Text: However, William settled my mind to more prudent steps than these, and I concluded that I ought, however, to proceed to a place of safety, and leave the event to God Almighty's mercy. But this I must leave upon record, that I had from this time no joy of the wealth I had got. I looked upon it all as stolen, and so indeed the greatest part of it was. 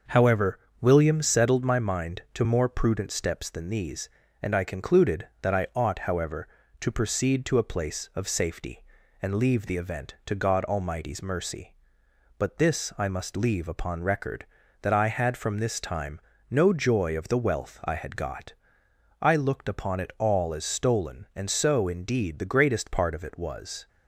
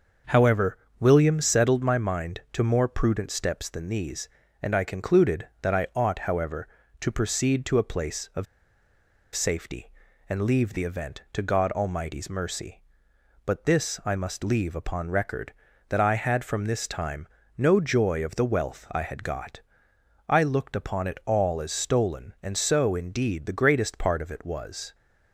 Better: first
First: starts louder than the rest; noticeable; until 1.2 s; 6 dB // pauses between "time" and "no"; slight; at 16.1 s; 0.32 s long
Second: starts louder than the rest; noticeable; until 1.4 s; 6 dB // pauses between "of" and "safety"; noticeable; at 8.4 s; 0.89 s long // pauses between "time" and "no"; slight; at 17.2 s; 0.32 s long

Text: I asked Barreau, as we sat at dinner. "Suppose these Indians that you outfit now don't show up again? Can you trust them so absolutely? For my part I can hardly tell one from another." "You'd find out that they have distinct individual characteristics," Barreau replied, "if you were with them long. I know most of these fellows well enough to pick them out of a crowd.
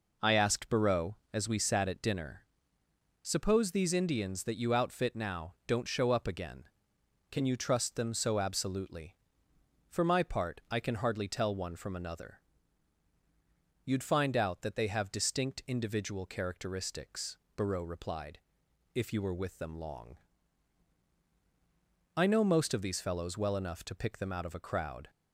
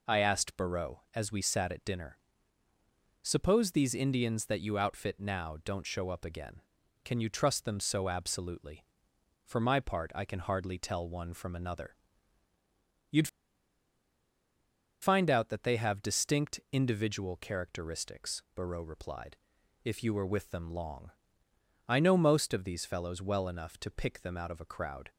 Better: first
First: none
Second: pauses between "You'd" and "find"; strong; at 13.2 s; 1.7 s long

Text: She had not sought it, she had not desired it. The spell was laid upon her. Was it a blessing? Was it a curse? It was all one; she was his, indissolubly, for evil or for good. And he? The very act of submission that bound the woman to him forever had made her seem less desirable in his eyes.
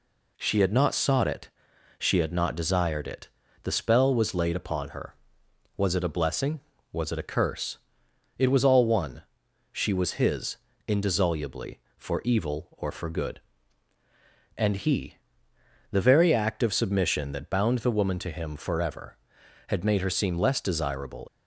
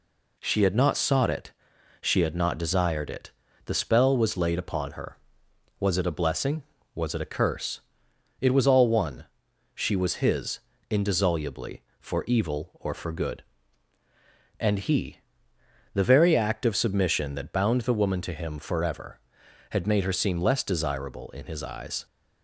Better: second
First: stops before "in his eyes"; at 21.2 s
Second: none

